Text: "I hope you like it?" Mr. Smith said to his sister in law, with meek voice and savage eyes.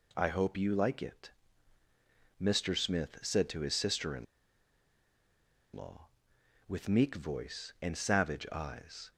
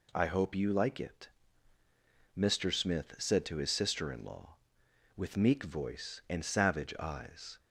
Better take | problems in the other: second | pauses between "in" and "law"; strong; at 4.2 s; 1.5 s long

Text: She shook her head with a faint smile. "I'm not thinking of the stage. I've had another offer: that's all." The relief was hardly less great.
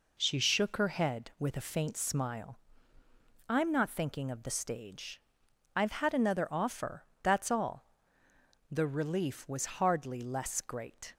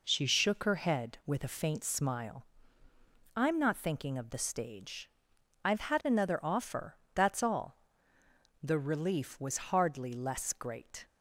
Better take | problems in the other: neither | none

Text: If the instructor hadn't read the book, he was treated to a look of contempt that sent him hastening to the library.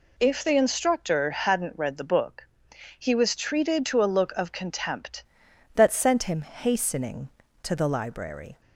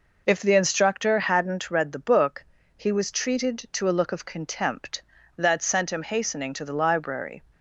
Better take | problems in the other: second | changes voice at "that"; from 5.7 s on; 2.9 s long

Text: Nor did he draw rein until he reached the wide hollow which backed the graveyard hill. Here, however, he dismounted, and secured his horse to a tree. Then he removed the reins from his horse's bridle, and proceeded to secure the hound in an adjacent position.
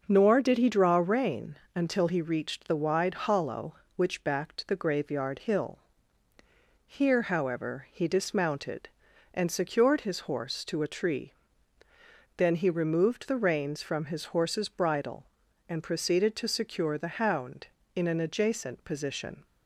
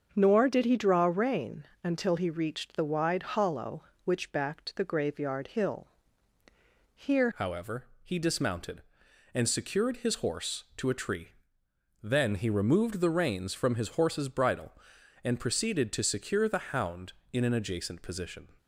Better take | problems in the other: first | starts louder than the rest; until 1.1 s; 6.5 dB // pauses between "rein" and "until"; slight; at 1.6 s; 0.18 s long; slight in the first // changes voice at "however"; from 7.3 s on; 11.1 s long

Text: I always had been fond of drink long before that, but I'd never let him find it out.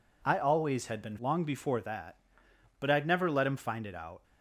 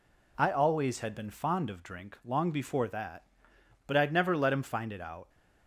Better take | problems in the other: second | skips "fond of drink"; at 1.1 s

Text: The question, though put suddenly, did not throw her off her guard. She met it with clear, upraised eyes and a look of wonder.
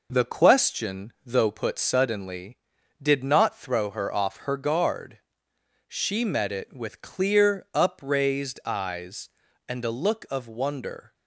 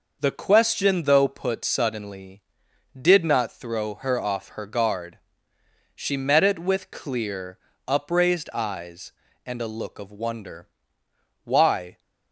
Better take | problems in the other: first | goes on to say "Why"; from 11.4 s on; 0.56 s long

